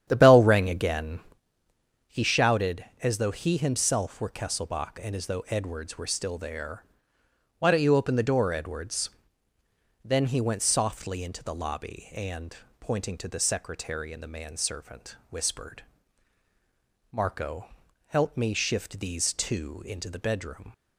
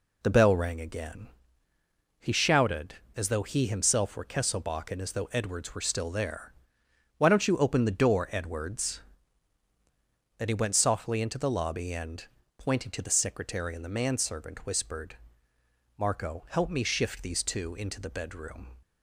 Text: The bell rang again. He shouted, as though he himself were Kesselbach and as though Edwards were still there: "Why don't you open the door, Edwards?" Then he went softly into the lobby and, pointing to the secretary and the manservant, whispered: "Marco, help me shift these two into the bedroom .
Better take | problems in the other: second | starts louder than the rest; strong; until 1.4 s; 9.5 dB

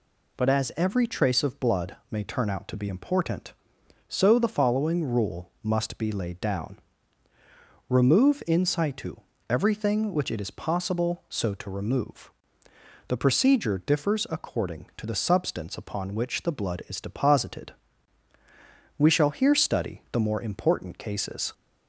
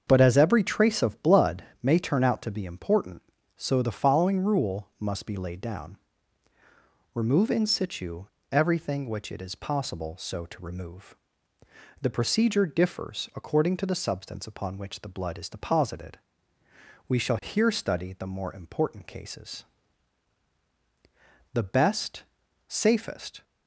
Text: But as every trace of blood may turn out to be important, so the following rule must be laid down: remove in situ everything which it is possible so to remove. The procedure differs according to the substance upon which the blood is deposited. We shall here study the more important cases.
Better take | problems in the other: first | starts louder than the rest; until 1.0 s; 7 dB // pauses between "blood" and "may"; slight; at 1.6 s; 0.20 s long; slight in the first // pauses between "situ" and "everything"; slight; at 8.2 s; 0.26 s long; slight in the first // goes on to say "The best safest"; strong; from 21.5 s on; 1.9 s long

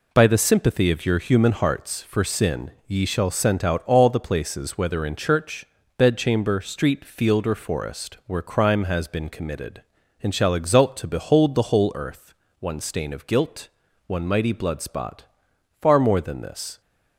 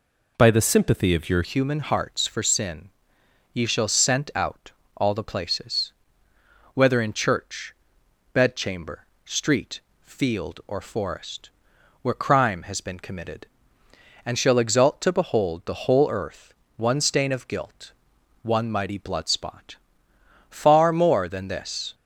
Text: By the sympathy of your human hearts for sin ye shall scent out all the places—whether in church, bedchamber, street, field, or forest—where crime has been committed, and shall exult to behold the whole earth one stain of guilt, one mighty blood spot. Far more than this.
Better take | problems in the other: first | changes voice at "human"; from 1.4 s on; 20.5 s long // pauses between "sin" and "ye"; noticeable; at 2.8 s; 0.64 s long // pauses between "out" and "all"; slight; at 4.7 s; 0.24 s long // pauses between "earth" and "one"; slight; at 16.5 s; 0.22 s long; slight in the first

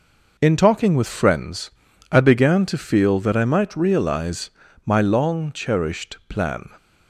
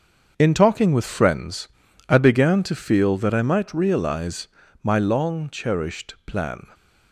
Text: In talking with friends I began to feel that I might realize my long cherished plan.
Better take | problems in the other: first | gets quieter; strong; throughout; 8 dB // pauses between "friends" and "I"; at 1.6 s; 0.40 s long; also in the first // pauses between "realize" and "my"; slight; at 4.4 s; 0.34 s long; slight in the first

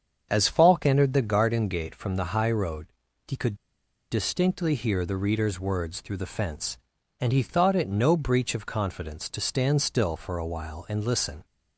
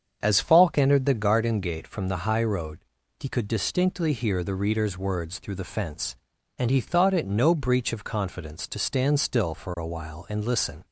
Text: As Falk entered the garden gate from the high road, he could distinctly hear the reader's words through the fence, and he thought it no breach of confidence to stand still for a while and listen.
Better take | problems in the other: second | starts louder than the rest; strong; until 1.3 s; 7 dB; strong in the second // pauses between "could" and "distinctly"; noticeable; at 3.5 s; 0.56 s long

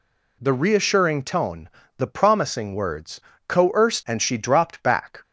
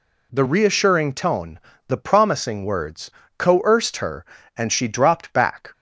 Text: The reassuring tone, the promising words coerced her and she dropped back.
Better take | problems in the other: second | pauses between "words" and "coerced"; slight; at 3.2 s; 0.28 s long; slight in the second // skips "her"; at 4.0 s

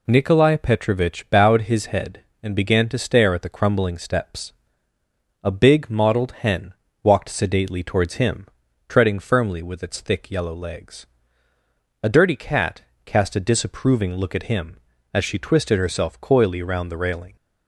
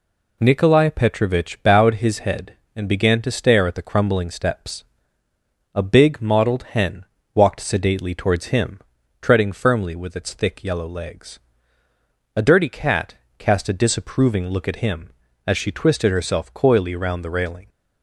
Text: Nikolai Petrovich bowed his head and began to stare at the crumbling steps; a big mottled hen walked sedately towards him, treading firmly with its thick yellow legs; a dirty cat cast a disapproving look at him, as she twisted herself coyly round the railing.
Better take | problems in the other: neither | pauses between "hen" and "walked"; slight; the same in both // pauses between "cat" and "cast"; slight; the same in both

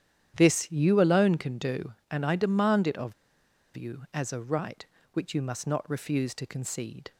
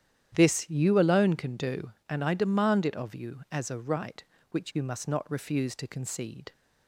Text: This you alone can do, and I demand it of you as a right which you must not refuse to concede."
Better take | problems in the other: second | starts louder than the rest; strong; until 1.3 s; 10 dB; strong in the second // pauses between "of" and "you"; noticeable; at 3.1 s; 0.61 s long

